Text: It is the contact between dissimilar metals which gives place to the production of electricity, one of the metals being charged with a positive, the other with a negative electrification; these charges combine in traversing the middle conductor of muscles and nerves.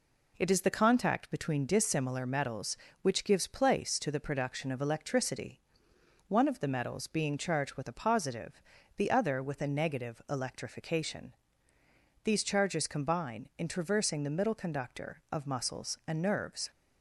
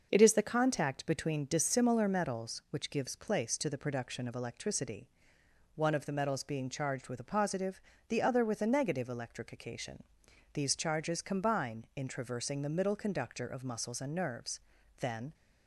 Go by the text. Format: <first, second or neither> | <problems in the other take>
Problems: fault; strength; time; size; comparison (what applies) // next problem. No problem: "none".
first | starts louder than the rest; noticeable; until 1.1 s; 6 dB // goes on to say "Then"; slight; from 14.9 s on; 0.34 s long